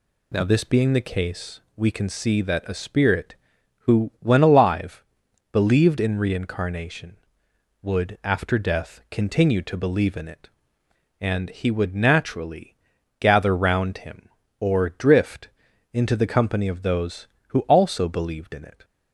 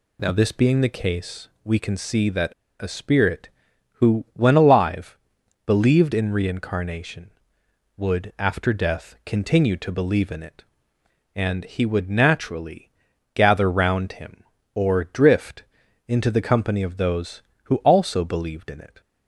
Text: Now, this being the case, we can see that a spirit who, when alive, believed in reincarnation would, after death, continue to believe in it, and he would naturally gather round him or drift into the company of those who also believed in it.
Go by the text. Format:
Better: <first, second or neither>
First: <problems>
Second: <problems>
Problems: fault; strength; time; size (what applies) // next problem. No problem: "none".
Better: first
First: pauses between "naturally" and "gather"; at 12.7 s; 0.44 s long // pauses between "drift" and "into"; at 15.4 s; 0.42 s long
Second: pauses between "that" and "a"; slight; at 2.5 s; 0.28 s long // pauses between "naturally" and "gather"; at 12.9 s; 0.44 s long // pauses between "drift" and "into"; at 15.6 s; 0.42 s long